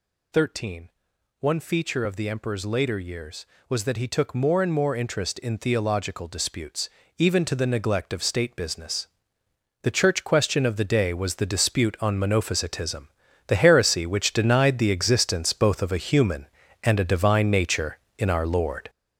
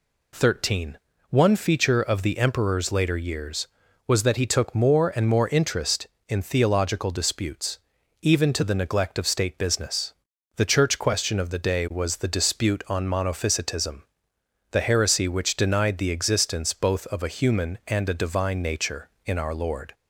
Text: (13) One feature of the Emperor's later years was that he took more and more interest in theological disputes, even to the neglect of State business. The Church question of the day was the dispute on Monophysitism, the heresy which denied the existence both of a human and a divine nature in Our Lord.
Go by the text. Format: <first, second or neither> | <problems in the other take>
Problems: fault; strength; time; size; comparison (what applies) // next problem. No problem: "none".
second | gets louder; strong; throughout; 7.5 dB